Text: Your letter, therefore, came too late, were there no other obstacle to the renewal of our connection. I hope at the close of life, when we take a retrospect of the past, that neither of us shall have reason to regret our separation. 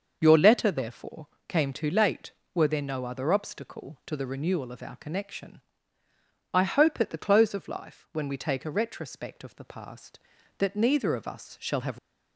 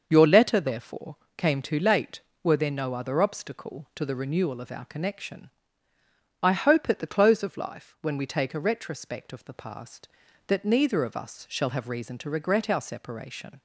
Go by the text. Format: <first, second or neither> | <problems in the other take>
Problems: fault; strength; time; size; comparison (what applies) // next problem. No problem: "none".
second | starts louder than the rest; until 1.2 s; 6.5 dB; also in the second // stops before "reason to regret our separation"; at 11.9 s